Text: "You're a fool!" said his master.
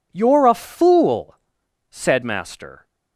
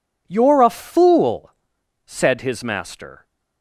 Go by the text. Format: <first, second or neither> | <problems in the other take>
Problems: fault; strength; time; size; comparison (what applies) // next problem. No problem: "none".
second | skips "his"; at 2.2 s